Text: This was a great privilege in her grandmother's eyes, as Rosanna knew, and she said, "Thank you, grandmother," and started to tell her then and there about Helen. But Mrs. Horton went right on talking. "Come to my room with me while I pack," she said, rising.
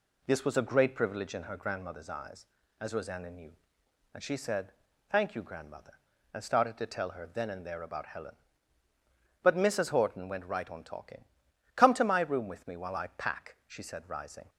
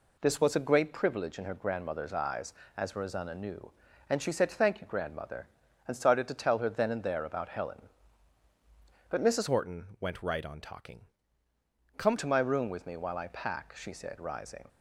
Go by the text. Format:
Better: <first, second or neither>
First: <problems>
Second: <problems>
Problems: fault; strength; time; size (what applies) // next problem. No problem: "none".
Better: first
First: none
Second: changes voice from "Horton" to "Come"; from 9.4 to 12.1 s; 2.7 s long